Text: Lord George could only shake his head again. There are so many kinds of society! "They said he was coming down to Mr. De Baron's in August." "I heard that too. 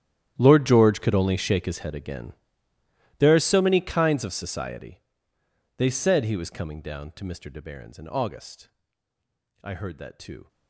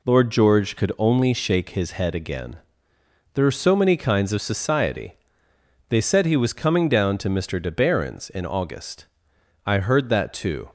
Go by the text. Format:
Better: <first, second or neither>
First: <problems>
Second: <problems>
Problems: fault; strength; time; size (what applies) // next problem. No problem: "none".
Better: second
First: gets quieter; strong; throughout; 19 dB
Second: none